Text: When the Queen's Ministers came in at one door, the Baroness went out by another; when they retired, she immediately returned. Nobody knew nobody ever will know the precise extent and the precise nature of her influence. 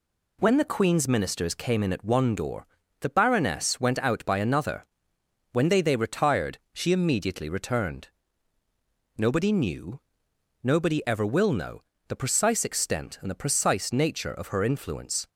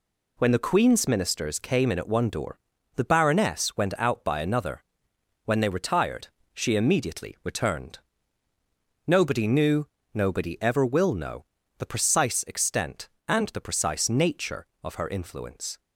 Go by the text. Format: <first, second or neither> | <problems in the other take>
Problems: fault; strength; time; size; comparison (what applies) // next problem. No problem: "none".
second | says "they" twice; at 5.8 s // pauses between "knew" and "nobody"; noticeable; at 9.9 s; 0.64 s long; slight in the second // pauses between "know" and "the"; slight; at 11.8 s; 0.26 s long; slight in the second